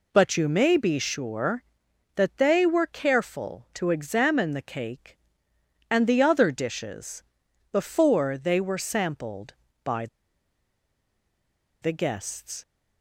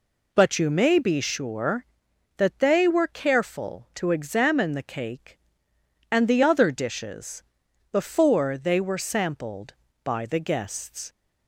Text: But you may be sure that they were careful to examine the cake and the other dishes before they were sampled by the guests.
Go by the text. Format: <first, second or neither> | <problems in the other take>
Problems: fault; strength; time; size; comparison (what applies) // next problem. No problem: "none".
second | pauses between "dishes" and "before"; noticeable; at 7.2 s; 0.48 s long; noticeable in the second // pauses between "by" and "the"; strong; at 10.0 s; 1.7 s long